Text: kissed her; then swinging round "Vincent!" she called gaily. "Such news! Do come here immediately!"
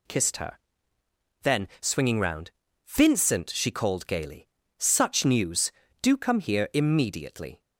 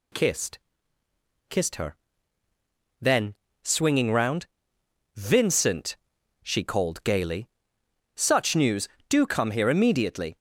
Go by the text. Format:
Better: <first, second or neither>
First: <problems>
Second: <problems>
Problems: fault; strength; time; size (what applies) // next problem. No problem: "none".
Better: first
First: pauses between "round" and "Vincent"; slight; at 2.5 s; 0.36 s long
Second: says "kissed" twice; at 1.4 s // pauses between "then" and "swinging"; slight; at 3.3 s; 0.28 s long // pauses between "round" and "Vincent"; noticeable; at 4.4 s; 0.70 s long